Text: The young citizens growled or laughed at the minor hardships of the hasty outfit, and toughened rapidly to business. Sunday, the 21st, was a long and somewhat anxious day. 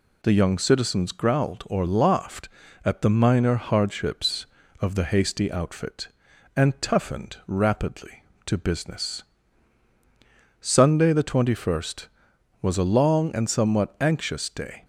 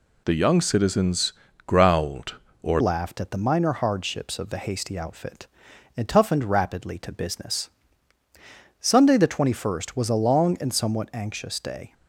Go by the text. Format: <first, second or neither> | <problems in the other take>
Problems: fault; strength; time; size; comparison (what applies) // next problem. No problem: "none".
first | pauses between "citizens" and "growled"; slight; at 1.3 s; 0.32 s long // changes voice at "laughed"; from 2.7 s on; 9.2 s long